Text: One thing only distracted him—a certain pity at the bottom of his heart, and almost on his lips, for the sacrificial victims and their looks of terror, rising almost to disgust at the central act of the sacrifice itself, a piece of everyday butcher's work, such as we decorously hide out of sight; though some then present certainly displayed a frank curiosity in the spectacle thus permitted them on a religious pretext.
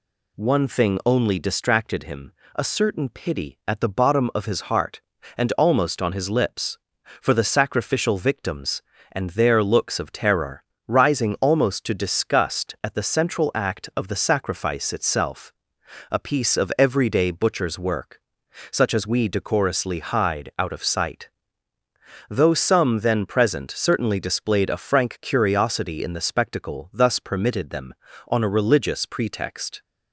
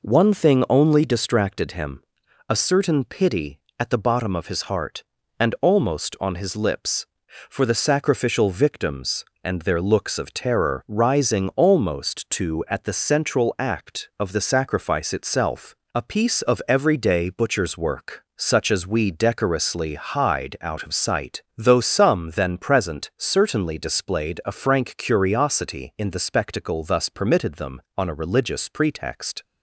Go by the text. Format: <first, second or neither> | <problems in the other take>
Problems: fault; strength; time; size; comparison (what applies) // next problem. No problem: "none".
first | skips "disgust"; at 12.6 s